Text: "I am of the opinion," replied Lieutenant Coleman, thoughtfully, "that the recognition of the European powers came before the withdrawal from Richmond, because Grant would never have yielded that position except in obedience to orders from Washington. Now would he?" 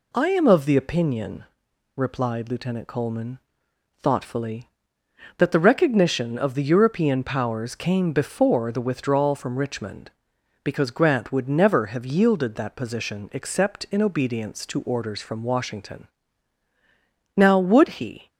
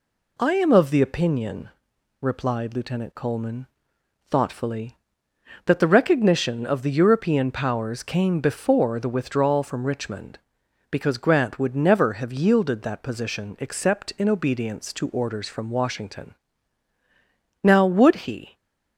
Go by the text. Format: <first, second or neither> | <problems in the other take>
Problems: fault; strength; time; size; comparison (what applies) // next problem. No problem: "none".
neither | none